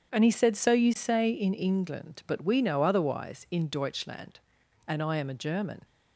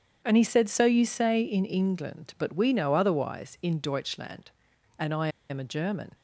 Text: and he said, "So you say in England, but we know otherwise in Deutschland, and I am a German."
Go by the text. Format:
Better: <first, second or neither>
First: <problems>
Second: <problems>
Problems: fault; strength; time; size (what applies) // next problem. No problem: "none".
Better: first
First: starts louder than the rest; strong; until 1.1 s; 8 dB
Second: starts louder than the rest; strong; until 1.2 s; 8 dB // pauses between "I" and "am"; slight; at 5.2 s; 0.21 s long